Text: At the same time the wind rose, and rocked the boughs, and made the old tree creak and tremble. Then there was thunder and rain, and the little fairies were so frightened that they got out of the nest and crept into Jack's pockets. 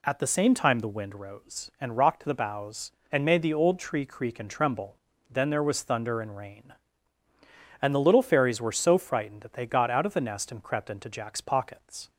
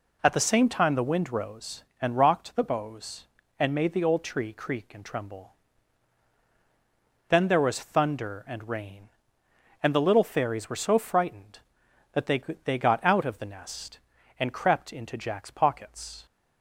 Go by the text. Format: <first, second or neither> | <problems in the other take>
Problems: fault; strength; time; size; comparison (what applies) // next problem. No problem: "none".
first | says "they" twice; at 12.6 s